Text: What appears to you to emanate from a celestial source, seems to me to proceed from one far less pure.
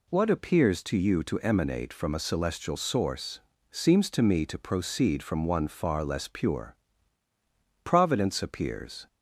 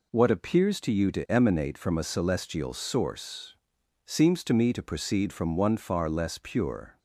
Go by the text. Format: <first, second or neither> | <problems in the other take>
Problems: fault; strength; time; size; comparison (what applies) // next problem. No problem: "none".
second | goes on to say "Providence appears"; noticeable; from 7.8 s on; 1.2 s long